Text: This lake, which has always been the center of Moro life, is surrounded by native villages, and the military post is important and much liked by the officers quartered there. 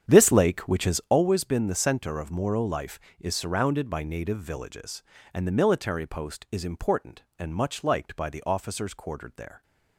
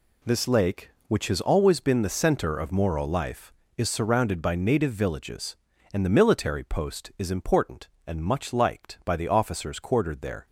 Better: second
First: starts louder than the rest; strong; until 1.2 s; 8.5 dB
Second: none

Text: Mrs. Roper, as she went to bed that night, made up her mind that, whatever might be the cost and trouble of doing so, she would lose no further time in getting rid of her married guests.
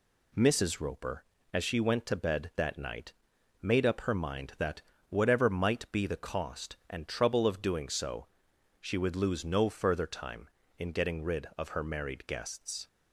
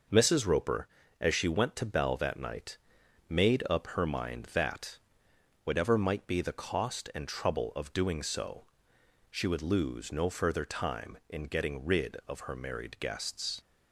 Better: first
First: none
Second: says "bell" for "bed"; at 1.8 s

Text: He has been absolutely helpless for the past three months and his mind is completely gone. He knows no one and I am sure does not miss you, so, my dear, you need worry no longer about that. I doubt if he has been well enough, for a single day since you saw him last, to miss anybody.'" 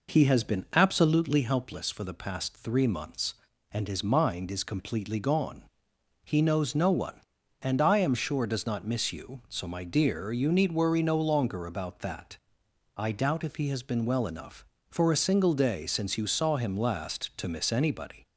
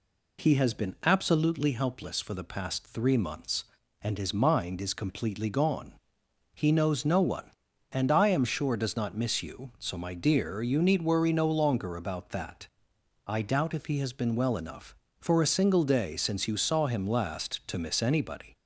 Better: second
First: starts louder than the rest; noticeable; until 1.8 s; 4.5 dB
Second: none

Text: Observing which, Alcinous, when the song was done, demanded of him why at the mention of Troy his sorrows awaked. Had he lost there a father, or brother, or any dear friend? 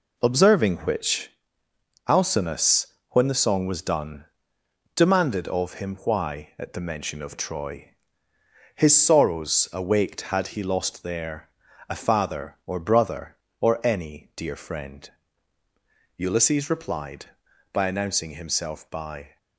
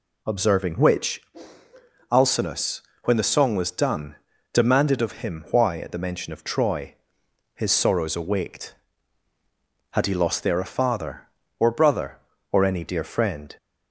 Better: second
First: pauses between "Troy" and "his"; noticeable; at 7.9 s; 0.84 s long // pauses between "there" and "a"; at 11.4 s; 0.38 s long // goes on to say "Ulysses replied by announcing himself by"; strong; from 16.1 s on; 3.2 s long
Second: pauses between "Troy" and "his"; noticeable; at 6.9 s; 0.60 s long

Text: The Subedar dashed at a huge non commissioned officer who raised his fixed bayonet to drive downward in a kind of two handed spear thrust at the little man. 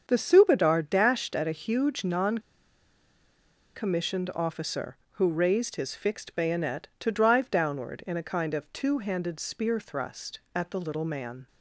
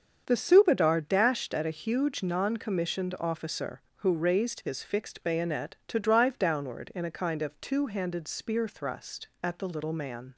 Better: second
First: starts louder than the rest; strong; until 1.0 s; 7 dB // pauses between "non" and "commissioned"; strong; at 2.3 s; 1.3 s long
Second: starts louder than the rest; strong; until 1.2 s; 7 dB

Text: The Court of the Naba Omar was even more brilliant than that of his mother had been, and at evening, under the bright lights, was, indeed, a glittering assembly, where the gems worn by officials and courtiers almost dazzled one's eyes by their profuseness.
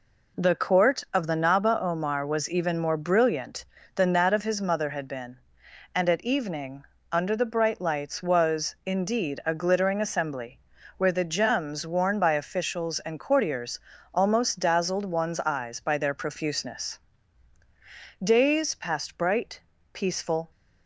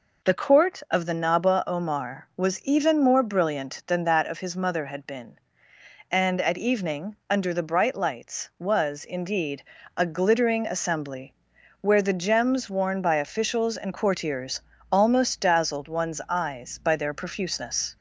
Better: second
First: pauses between "courtiers" and "almost"; slight; at 13.7 s; 0.34 s long // goes on to say "Days passed bright peaceful"; strong; from 18.2 s on; 2.3 s long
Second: pauses between "courtiers" and "almost"; slight; at 14.6 s; 0.32 s long

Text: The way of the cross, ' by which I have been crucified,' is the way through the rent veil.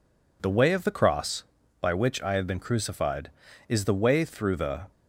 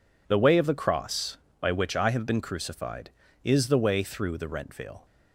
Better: second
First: stops before "rent veil"; at 4.9 s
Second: none

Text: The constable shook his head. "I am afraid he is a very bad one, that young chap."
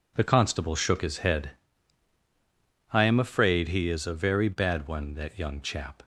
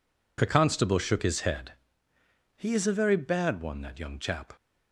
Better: first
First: none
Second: skips "I am afraid"; at 2.1 s

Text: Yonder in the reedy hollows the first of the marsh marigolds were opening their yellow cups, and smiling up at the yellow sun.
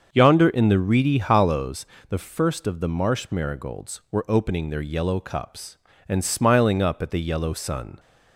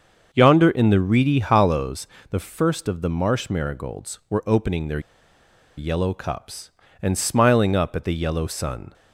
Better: first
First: starts louder than the rest; until 1.1 s; 6.5 dB // pauses between "hollows" and "the"; slight; at 1.8 s; 0.22 s long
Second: starts louder than the rest; until 1.3 s; 6.5 dB // pauses between "hollows" and "the"; slight; at 2.0 s; 0.22 s long // pauses between "their" and "yellow"; noticeable; at 4.9 s; 0.77 s long

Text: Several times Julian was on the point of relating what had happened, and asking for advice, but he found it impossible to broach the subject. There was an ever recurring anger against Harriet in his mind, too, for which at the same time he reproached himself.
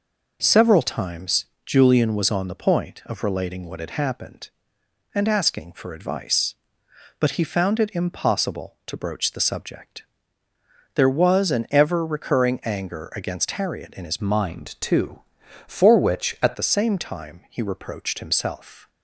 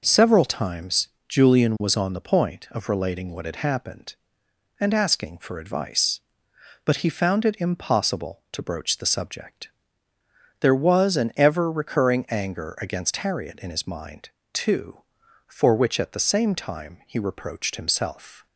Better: second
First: pauses between "times" and "Julian"; slight; at 1.4 s; 0.22 s long // changes voice from "mind" to "at"; from 14.2 to 16.5 s; 2.3 s long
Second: pauses between "times" and "Julian"; slight; at 1.0 s; 0.22 s long

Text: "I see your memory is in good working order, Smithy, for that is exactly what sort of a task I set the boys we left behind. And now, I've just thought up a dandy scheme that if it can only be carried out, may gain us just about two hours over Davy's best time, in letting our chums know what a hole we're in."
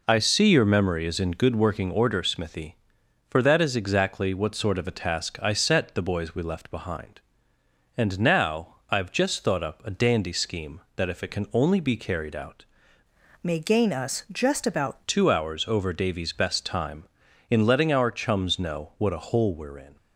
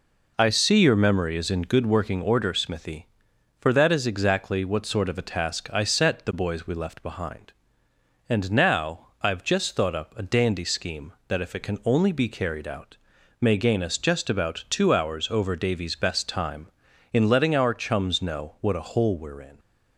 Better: second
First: changes voice from "may" to "about"; from 13.4 to 14.9 s; 1.5 s long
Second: none

